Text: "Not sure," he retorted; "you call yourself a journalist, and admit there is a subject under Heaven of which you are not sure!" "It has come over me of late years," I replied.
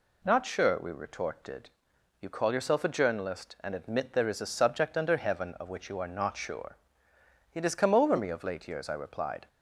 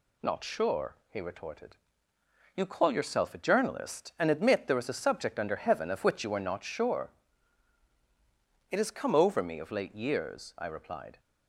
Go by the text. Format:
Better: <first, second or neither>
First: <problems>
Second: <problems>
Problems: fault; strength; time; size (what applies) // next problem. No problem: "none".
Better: second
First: says "we" for "he"; at 0.8 s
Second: none